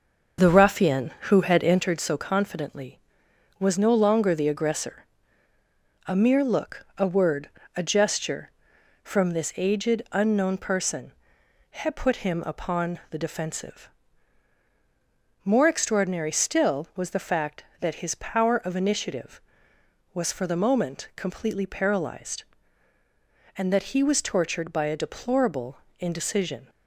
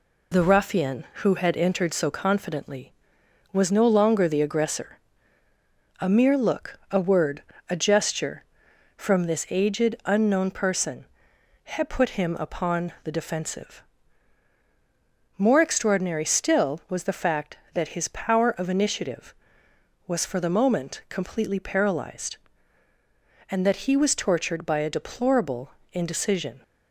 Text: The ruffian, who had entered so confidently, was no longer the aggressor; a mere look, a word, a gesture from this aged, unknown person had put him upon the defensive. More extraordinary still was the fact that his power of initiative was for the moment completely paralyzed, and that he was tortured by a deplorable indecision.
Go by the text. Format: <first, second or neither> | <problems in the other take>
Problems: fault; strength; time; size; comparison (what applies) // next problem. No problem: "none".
second | starts louder than the rest; until 1.9 s; 6.5 dB // pauses between "deplorable" and "indecision"; slight; at 25.7 s; 0.20 s long; slight in the second